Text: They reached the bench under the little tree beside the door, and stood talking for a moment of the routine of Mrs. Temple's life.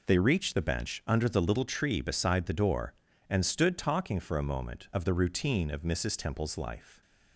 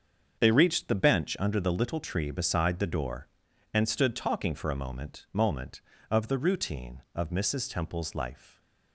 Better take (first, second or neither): first